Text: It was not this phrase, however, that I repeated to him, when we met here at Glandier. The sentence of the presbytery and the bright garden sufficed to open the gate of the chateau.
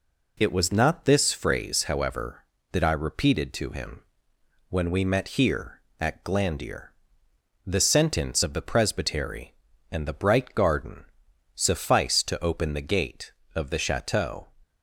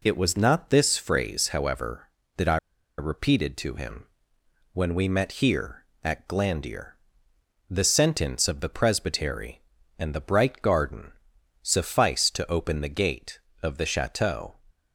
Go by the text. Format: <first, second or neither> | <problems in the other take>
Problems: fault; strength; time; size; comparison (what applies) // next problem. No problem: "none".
first | pauses between "I" and "repeated"; at 2.5 s; 0.41 s long // pauses between "garden" and "sufficed"; noticeable; at 11.1 s; 0.50 s long; noticeable in the first